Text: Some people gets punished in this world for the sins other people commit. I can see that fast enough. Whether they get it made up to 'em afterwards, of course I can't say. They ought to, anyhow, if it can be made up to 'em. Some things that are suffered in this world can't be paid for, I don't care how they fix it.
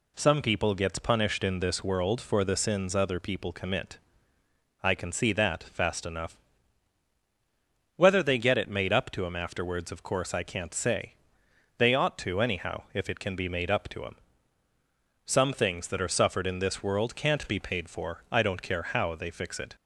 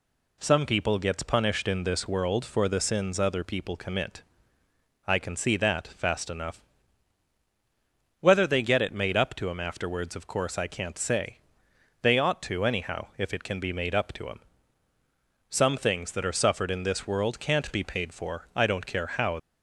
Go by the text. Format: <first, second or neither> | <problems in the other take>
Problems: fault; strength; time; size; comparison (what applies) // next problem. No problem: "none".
first | stops before "they fix it"; at 19.3 s